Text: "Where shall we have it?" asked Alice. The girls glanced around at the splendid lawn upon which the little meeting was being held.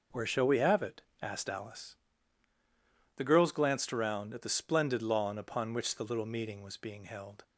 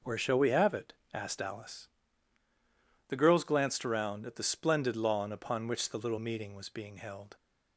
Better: neither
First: none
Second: none

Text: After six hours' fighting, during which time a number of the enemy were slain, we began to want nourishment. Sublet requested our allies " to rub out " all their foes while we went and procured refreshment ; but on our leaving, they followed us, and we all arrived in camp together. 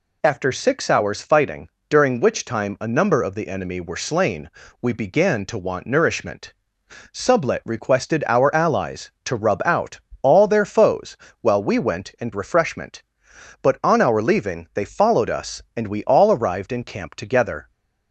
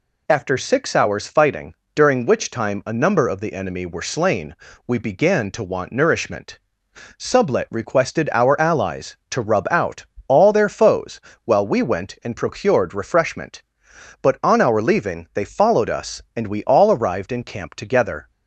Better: second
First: pauses between "foes" and "while"; slight; at 11.1 s; 0.24 s long // skips "procured"; at 12.3 s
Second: pauses between "foes" and "while"; slight; at 11.2 s; 0.24 s long

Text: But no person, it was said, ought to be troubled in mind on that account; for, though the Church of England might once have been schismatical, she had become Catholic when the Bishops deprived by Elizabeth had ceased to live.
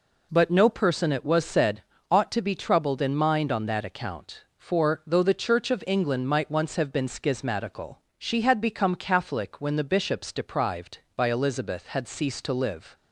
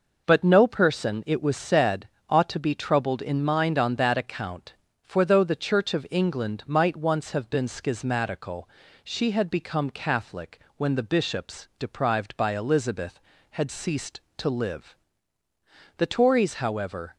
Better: first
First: none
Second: pauses between "Catholic" and "when"; slight; at 10.5 s; 0.18 s long // goes on to say "The Tories however"; noticeable; from 15.9 s on; 1.1 s long

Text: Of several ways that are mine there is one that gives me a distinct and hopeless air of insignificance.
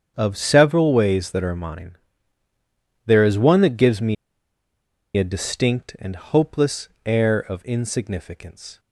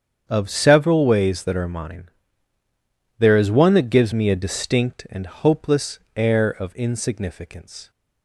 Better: second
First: starts louder than the rest; strong; until 1.1 s; 8 dB // pauses between "mine" and "there"; at 1.9 s; 1.1 s long // pauses between "me" and "a"; at 4.1 s; 1.0 s long // pauses between "hopeless" and "air"; slight; at 6.8 s; 0.18 s long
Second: starts louder than the rest; strong; until 1.2 s; 8 dB // pauses between "mine" and "there"; at 2.0 s; 1.1 s long // pauses between "hopeless" and "air"; slight; at 5.9 s; 0.18 s long

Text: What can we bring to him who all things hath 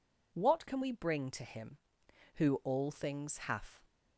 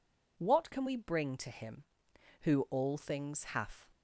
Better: neither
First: none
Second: none

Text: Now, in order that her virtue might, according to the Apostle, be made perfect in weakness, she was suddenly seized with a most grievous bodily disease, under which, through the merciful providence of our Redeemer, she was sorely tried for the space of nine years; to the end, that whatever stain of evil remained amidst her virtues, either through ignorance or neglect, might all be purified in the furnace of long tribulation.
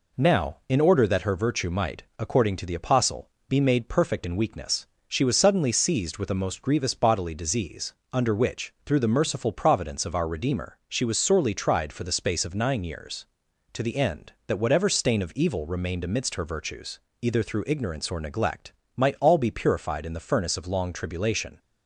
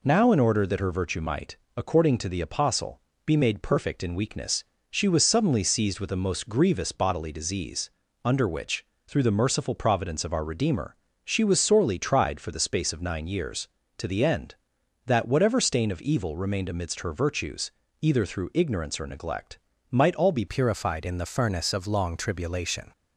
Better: first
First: none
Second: changes voice at "purified"; from 20.4 s on; 2.5 s long

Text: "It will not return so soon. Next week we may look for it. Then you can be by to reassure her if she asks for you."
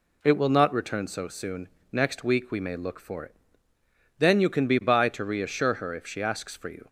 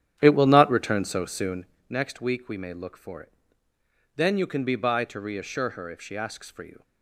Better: first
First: none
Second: starts louder than the rest; strong; until 1.8 s; 10 dB

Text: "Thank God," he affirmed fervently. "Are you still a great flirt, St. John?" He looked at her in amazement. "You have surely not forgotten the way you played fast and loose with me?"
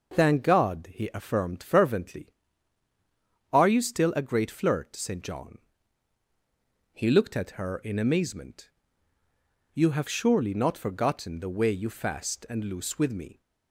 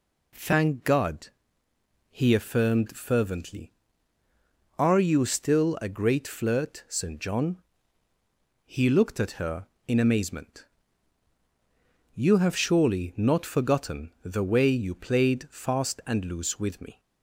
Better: second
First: skips "played"; at 11.8 s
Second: none

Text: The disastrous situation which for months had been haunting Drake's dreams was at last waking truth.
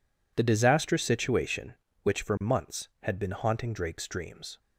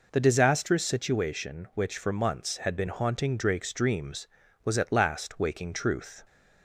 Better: second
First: stops before "was at last waking truth"; at 4.5 s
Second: none

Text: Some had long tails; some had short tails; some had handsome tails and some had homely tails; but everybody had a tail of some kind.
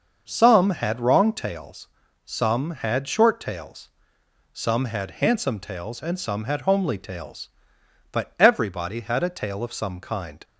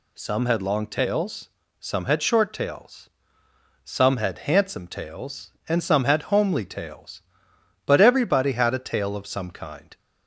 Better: second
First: starts louder than the rest; until 1.2 s; 6.5 dB // says "wrong" for "long"; at 0.9 s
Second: none

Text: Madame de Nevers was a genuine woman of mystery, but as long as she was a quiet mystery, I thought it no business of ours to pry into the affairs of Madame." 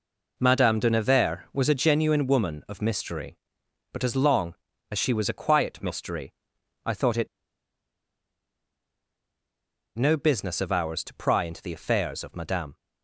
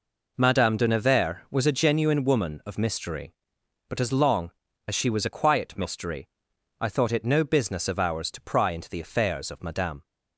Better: second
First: pauses between "it" and "no"; strong; at 7.2 s; 2.7 s long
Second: none

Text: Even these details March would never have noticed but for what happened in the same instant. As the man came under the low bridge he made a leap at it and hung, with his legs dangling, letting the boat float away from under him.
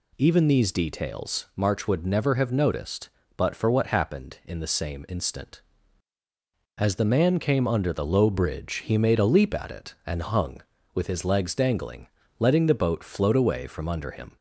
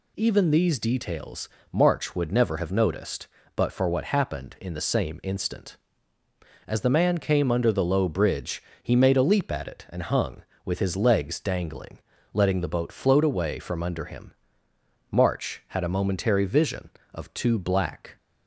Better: first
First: none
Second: pauses between "details" and "March"; slight; at 1.4 s; 0.24 s long // pauses between "bridge" and "he"; slight; at 8.6 s; 0.20 s long // goes on to say "March had a momentary vision of two black"; strong; from 15.1 s on; 3.0 s long

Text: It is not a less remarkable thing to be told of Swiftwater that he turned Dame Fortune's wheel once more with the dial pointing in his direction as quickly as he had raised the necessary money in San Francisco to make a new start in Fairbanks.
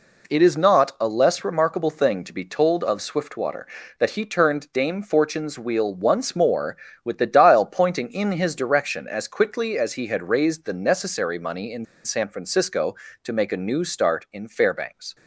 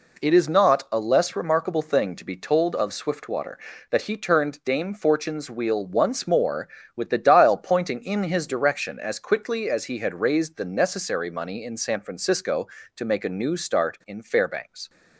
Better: second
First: pauses between "in" and "San"; slight; at 11.8 s; 0.19 s long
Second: none

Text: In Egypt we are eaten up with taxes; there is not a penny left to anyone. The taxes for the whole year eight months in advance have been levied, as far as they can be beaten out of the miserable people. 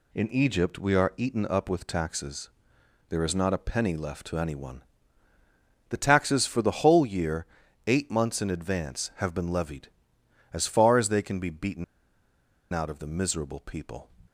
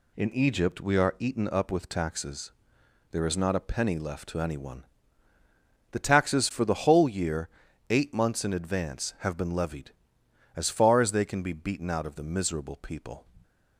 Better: second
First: pauses between "year" and "eight"; at 7.4 s; 0.42 s long // pauses between "beaten" and "out"; noticeable; at 11.8 s; 0.89 s long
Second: pauses between "year" and "eight"; at 7.4 s; 0.42 s long

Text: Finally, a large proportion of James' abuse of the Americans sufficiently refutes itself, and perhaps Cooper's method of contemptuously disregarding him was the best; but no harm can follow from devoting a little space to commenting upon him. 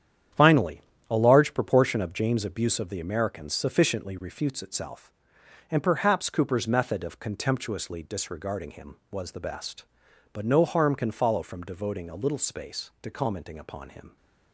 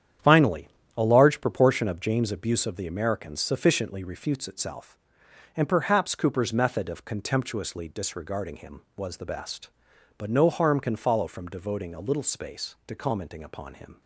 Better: neither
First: starts louder than the rest; strong; until 1.6 s; 9.5 dB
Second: starts louder than the rest; strong; until 1.5 s; 9.5 dB

